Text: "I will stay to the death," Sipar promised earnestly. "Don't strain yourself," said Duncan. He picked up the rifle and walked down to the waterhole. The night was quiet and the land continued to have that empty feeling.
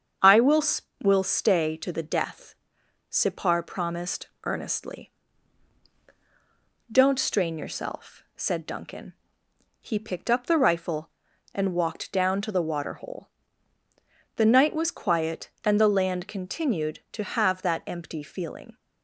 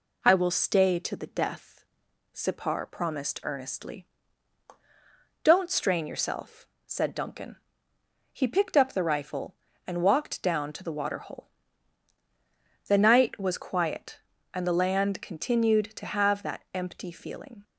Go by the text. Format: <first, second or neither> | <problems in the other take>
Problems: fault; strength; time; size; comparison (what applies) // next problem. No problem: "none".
second | starts louder than the rest; strong; until 1.6 s; 7.5 dB // says "will" twice; at 1.0 s // pauses between "promised" and "earnestly"; slight; at 4.2 s; 0.16 s long